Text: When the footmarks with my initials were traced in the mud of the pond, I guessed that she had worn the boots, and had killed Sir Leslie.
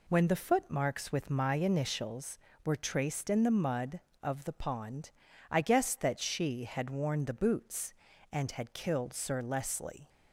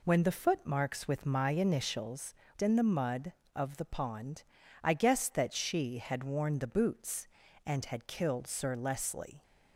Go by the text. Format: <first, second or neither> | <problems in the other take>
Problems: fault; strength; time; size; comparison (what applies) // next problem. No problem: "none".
first | skips "were traced"; at 2.4 s